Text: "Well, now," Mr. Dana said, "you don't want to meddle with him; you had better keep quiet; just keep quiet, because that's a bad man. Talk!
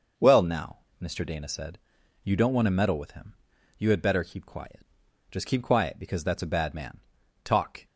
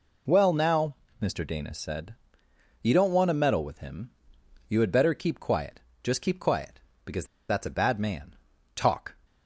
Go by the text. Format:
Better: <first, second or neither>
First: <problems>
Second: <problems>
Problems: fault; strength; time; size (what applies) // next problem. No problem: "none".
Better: first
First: none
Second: pauses between "because" and "that's"; slight; at 7.2 s; 0.24 s long